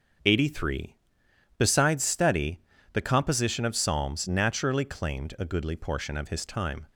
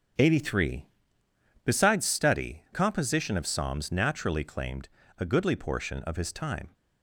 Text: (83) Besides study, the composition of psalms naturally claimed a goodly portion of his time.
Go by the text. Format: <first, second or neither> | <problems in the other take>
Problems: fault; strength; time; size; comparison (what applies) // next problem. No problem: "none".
first | starts louder than the rest; strong; until 1.9 s; 8 dB; also in the first // skips "the"; at 2.6 s // pauses between "claimed" and "a"; slight; at 4.8 s; 0.28 s long